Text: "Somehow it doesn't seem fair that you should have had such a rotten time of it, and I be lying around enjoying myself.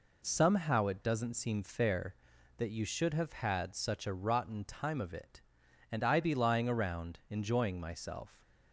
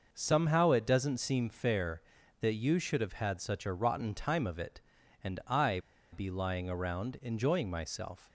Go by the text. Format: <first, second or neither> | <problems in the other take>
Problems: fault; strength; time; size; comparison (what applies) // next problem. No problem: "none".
first | pauses between "I" and "be"; slight; at 5.7 s; 0.33 s long